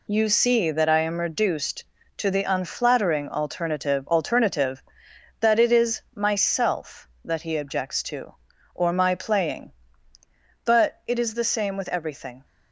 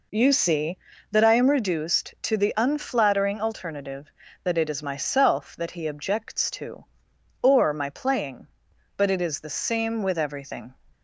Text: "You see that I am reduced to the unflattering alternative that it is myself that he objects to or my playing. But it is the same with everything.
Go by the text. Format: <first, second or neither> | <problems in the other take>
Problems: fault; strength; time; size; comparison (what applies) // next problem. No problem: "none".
second | says "alternative" twice; at 4.0 s // pauses between "is" and "myself"; slight; at 5.9 s; 0.16 s long